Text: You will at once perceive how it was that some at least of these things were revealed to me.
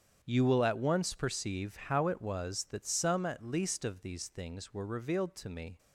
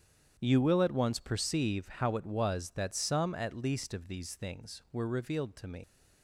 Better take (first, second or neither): first